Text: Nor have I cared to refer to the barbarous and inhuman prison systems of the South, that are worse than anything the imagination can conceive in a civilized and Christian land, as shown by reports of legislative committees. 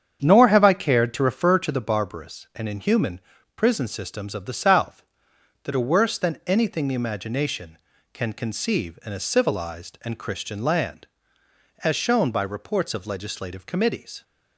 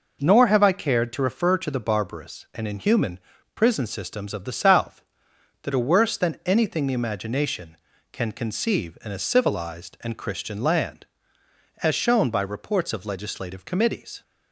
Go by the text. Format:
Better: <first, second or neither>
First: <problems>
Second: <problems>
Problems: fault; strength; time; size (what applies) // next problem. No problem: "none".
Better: second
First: starts louder than the rest; strong; until 1.9 s; 8 dB // pauses between "inhuman" and "prison"; slight; at 3.2 s; 0.34 s long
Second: pauses between "inhuman" and "prison"; slight; at 3.1 s; 0.34 s long